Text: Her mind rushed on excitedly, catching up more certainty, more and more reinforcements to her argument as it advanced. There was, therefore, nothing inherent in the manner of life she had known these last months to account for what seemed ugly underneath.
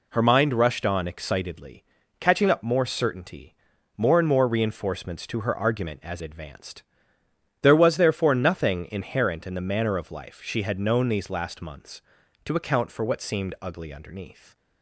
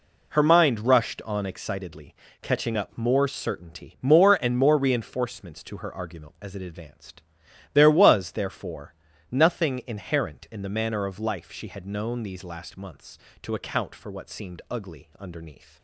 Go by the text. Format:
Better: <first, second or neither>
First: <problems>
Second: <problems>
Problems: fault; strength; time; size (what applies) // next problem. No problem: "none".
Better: second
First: skips "it"; at 6.2 s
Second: none